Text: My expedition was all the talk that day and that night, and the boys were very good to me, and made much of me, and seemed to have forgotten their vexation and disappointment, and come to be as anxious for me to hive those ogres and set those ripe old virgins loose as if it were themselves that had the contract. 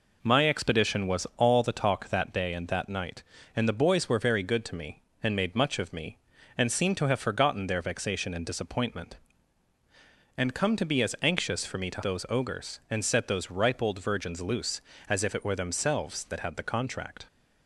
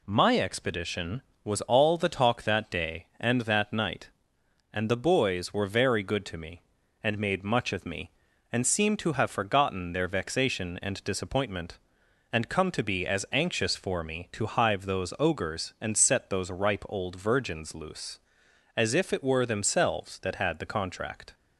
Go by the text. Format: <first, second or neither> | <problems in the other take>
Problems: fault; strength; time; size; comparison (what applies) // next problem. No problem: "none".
second | skips "hive"; at 12.0 s